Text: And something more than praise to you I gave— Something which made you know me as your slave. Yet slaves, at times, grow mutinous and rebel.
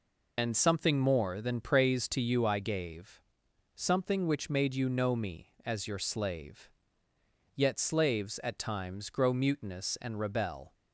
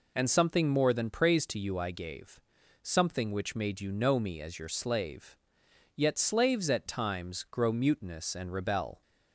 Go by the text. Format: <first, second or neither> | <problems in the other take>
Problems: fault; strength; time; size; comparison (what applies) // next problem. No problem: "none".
second | loses the start of "And"; at 0.3 s; 65 ms